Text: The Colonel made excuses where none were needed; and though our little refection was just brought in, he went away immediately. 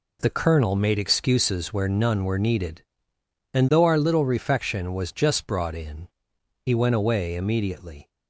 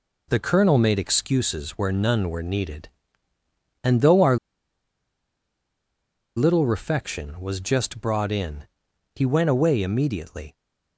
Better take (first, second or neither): first